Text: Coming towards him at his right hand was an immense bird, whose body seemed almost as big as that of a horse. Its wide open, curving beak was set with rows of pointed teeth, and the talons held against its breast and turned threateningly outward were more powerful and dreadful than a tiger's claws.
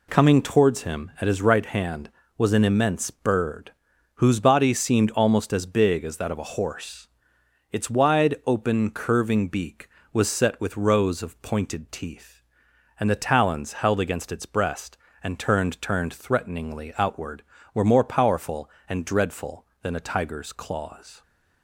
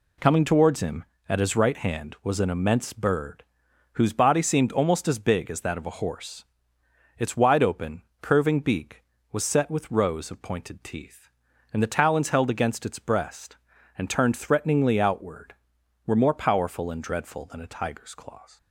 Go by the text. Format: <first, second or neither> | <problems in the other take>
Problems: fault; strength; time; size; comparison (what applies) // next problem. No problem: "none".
second | says "turned" twice; at 15.7 s